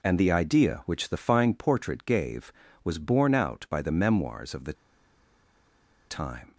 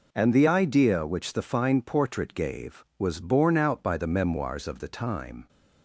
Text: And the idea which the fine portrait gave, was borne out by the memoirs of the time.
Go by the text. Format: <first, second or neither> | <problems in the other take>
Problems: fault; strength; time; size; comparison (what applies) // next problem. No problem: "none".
second | pauses between "the" and "time"; strong; at 4.7 s; 1.3 s long